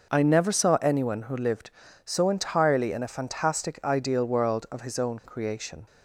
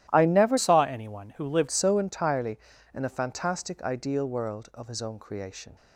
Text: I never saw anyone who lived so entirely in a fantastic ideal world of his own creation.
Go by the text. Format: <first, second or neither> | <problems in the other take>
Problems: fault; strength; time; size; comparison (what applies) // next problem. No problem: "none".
first | starts louder than the rest; strong; until 1.1 s; 13.5 dB; also in the first // changes voice from "saw" to "lived"; from 0.5 to 1.6 s; 1.1 s long